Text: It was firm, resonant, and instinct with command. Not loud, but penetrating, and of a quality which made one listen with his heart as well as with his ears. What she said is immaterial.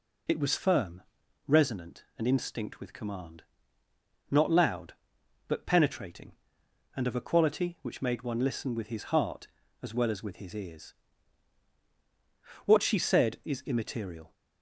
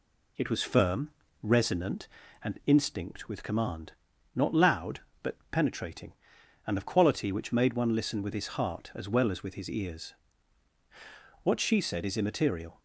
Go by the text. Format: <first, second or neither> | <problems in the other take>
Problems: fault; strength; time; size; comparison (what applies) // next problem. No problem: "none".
first | skips "a"; at 6.8 s